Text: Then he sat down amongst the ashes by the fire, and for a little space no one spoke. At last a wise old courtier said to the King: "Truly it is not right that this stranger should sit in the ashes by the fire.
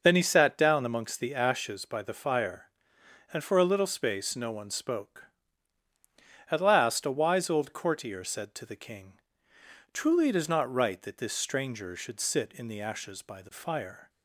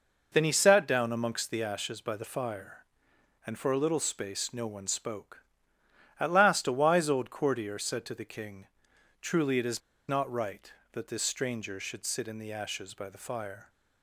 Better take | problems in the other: first | pauses between "is" and "not"; slight; at 9.7 s; 0.29 s long

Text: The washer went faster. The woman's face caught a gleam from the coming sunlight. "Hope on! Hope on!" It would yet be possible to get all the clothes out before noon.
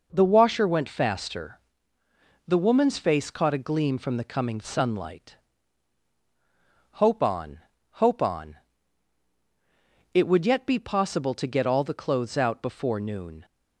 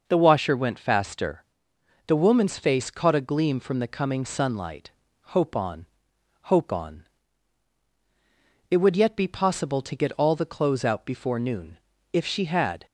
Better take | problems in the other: first | goes on to say "If she had"; noticeable; from 12.1 s on; 0.72 s long

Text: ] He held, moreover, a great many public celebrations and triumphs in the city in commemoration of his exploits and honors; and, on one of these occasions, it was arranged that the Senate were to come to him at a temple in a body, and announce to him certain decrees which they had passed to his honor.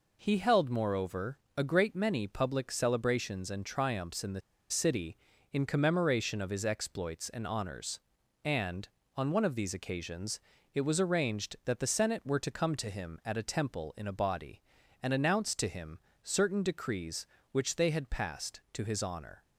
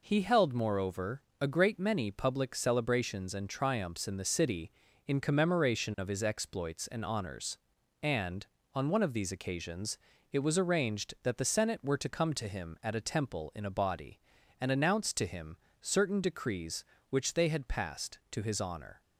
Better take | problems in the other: second | pauses between "the" and "city"; slight; at 4.4 s; 0.30 s long // pauses between "him" and "certain"; slight; at 15.9 s; 0.24 s long; slight in the second

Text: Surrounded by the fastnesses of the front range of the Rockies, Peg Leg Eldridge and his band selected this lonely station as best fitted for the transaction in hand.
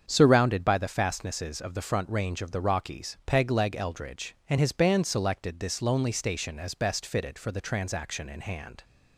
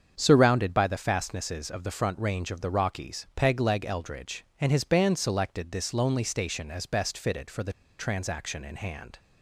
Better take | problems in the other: first | starts louder than the rest; strong; until 1.1 s; 7.5 dB; strong in the first // pauses between "the" and "transaction"; slight; at 7.7 s; 0.24 s long

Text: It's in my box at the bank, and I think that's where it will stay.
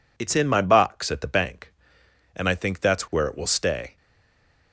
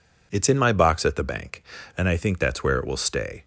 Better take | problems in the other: second | stays silent after the last word; slight; from 3.9 s on; 0.8 s long

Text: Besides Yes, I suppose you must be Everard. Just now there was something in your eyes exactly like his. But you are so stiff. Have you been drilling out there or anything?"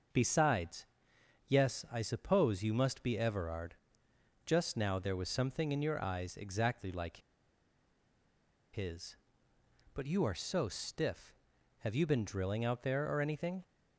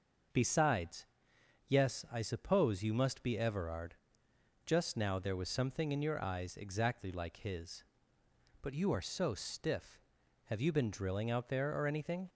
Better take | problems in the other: second | starts louder than the rest; noticeable; until 1.7 s; 6 dB; noticeable in the second // pauses between "Besides" and "Yes"; noticeable; at 0.8 s; 0.60 s long; noticeable in the second // pauses between "like" and "his"; strong; at 7.1 s; 1.5 s long

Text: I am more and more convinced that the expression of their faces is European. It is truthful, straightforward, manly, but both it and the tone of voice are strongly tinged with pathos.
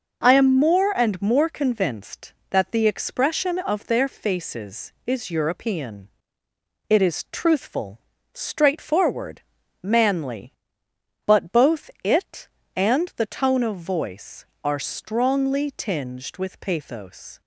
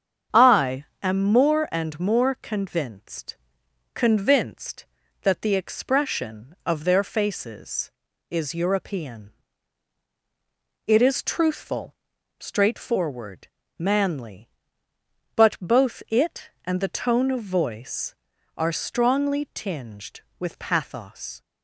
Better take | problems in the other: first | starts louder than the rest; strong; until 1.5 s; 7.5 dB // pauses between "I" and "am"; slight; at 0.8 s; 0.18 s long // says "convinced" twice; at 3.9 s

